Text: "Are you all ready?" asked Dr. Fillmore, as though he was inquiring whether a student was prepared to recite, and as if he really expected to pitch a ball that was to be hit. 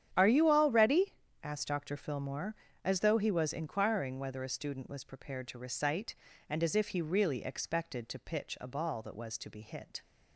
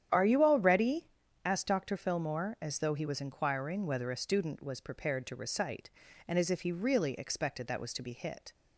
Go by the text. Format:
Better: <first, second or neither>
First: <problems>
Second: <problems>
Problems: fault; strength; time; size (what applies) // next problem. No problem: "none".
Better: first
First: starts louder than the rest; strong; until 1.1 s; 9.5 dB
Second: starts louder than the rest; strong; until 1.5 s; 9.5 dB // skips "to pitch a ball"; at 7.6 s